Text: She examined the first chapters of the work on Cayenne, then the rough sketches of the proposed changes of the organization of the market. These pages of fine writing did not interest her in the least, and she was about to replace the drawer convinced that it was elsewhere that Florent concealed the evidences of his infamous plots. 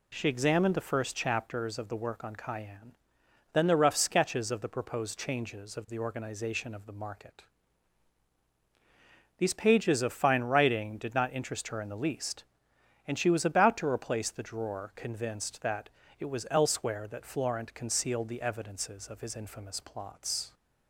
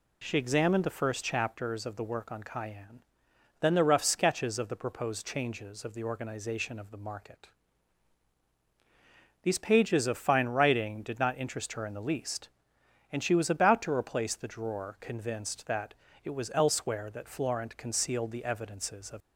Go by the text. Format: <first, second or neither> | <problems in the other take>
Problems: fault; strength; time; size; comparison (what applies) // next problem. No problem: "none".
first | pauses between "that" and "it"; slight; at 15.9 s; 0.28 s long; slight in the first // stops before "his infamous plots"; at 19.2 s